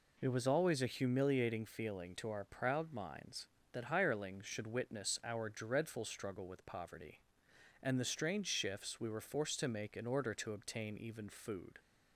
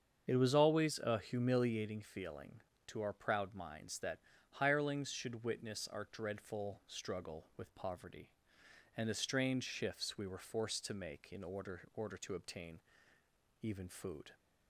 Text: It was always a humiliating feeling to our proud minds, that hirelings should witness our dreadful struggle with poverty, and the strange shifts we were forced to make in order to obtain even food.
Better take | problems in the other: first | starts louder than the rest; strong; until 1.3 s; 7 dB // pauses between "that" and "hirelings"; slight; at 4.1 s; 0.36 s long // says "order" twice; at 11.9 s // pauses between "obtain" and "even"; noticeable; at 12.7 s; 0.82 s long

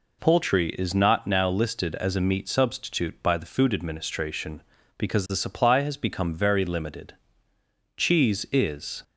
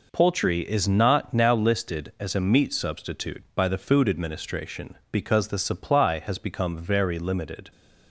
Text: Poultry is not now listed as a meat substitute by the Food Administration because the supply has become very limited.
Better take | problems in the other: second | goes on to say "Cheese is"; noticeable; from 7.9 s on; 1.0 s long

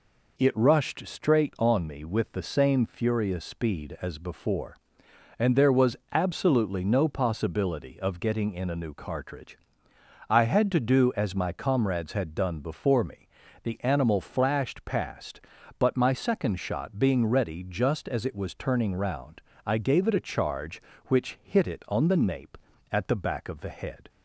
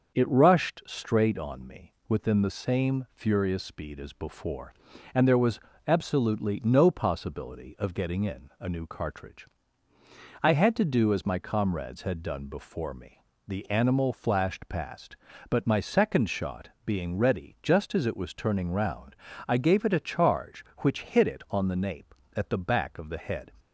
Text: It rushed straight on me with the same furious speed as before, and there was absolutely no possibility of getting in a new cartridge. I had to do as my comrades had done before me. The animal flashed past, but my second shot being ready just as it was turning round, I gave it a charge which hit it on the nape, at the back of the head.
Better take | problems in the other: first | starts louder than the rest; until 1.2 s; 6.5 dB // says "within" for "with"; at 2.0 s // pauses between "was" and "absolutely"; slight; at 5.5 s; 0.28 s long; slight in the first // pauses between "shot" and "being"; slight; at 16.6 s; 0.16 s long

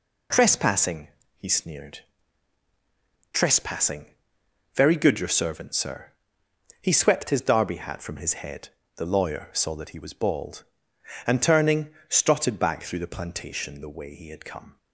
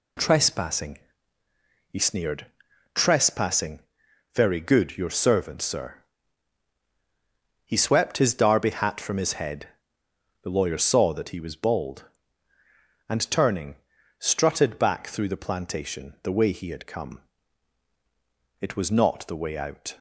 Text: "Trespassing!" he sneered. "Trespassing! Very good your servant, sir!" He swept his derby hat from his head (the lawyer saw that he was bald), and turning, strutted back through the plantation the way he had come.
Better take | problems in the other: first | goes on to say "It was not the way out"; from 18.5 s on; 1.3 s long

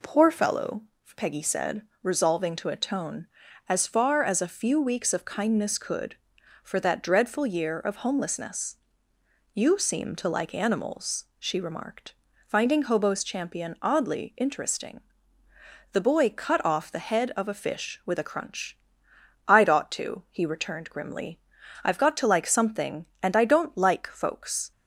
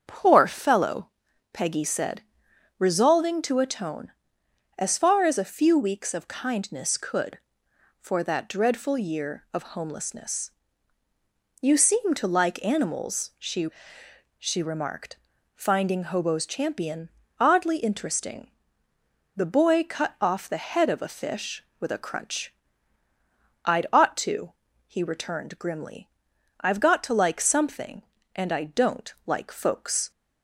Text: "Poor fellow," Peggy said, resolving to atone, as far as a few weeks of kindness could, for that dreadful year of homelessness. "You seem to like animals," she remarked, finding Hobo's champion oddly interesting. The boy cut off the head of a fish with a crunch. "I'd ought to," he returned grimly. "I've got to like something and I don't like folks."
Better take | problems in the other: first | starts louder than the rest; strong; until 1.5 s; 7.5 dB // says "she" twice; at 14.3 s // pauses between "champion" and "oddly"; slight; at 17.1 s; 0.28 s long

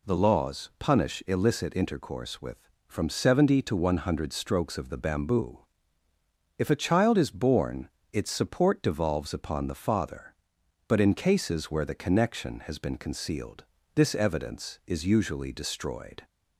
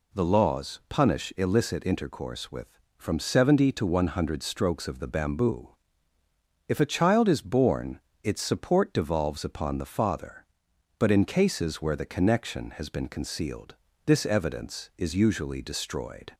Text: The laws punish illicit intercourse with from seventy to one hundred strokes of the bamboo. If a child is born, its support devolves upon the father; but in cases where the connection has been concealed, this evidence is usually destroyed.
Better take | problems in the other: neither | none

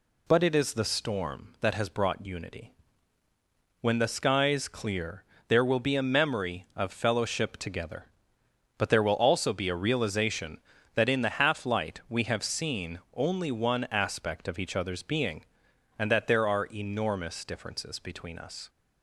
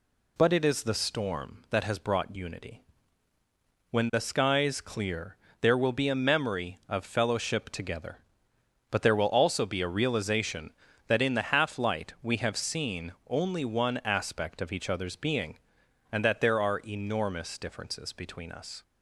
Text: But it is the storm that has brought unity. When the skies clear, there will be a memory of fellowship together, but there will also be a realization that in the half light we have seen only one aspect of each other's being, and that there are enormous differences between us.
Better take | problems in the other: neither | pauses between "seen" and "only"; slight; the same in both

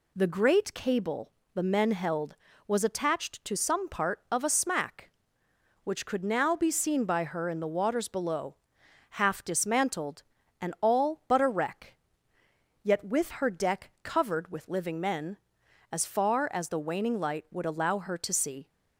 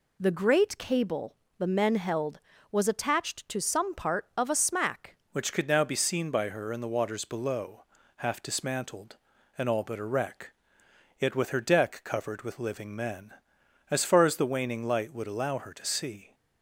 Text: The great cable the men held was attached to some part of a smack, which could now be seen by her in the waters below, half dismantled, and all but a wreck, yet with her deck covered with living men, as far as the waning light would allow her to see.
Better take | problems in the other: first | pauses between "cable" and "the"; slight; at 1.3 s; 0.24 s long; slight in the first // changes voice at "which"; from 5.3 s on; 11.0 s long

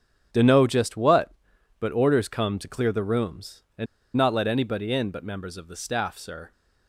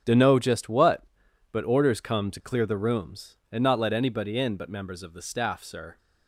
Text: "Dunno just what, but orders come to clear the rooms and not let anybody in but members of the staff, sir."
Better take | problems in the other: second | starts louder than the rest; strong; until 1.8 s; 8.5 dB; strong in the second // pauses between "and" and "not"; slight; at 3.8 s; 0.31 s long

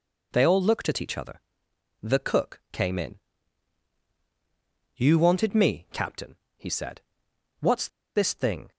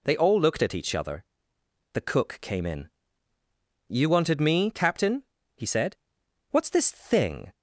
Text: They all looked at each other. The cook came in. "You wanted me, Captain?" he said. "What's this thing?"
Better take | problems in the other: second | pauses between "What's" and "this"; slight; at 7.8 s; 0.28 s long

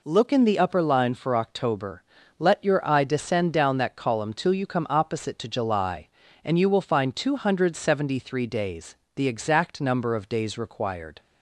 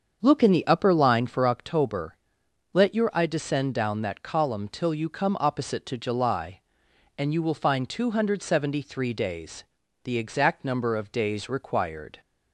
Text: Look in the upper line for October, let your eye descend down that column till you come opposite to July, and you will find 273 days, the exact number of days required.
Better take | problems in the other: first | starts louder than the rest; until 1.6 s; 7 dB

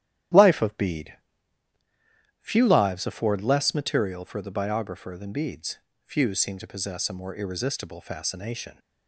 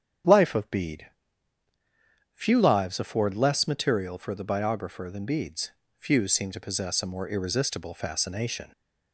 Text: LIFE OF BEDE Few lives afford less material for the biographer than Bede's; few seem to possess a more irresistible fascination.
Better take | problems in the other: second | gets quieter; strong; throughout; 9 dB // starts louder than the rest; strong; until 2.6 s; 11.5 dB; strong in the second // pauses between "BEDE" and "Few"; strong; at 1.1 s; 1.2 s long; strong in the second

